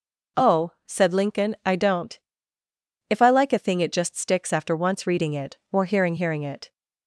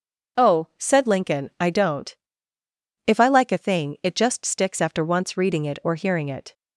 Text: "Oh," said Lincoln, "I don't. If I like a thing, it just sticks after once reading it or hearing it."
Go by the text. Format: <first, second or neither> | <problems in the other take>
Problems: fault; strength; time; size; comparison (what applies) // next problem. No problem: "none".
second | says "hearing" twice; at 6.1 s